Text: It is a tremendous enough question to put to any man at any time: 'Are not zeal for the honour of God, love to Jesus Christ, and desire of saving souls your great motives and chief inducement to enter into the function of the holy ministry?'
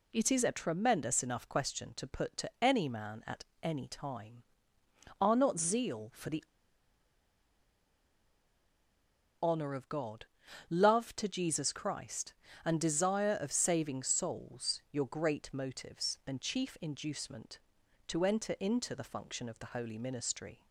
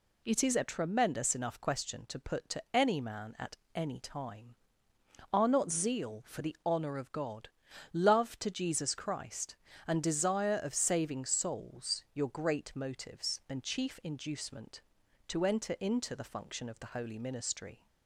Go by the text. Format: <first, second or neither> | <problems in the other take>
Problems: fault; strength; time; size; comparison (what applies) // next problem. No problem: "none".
second | pauses between "at" and "any"; slight; at 3.4 s; 0.18 s long; slight in the second // pauses between "the" and "honour"; strong; at 6.4 s; 2.9 s long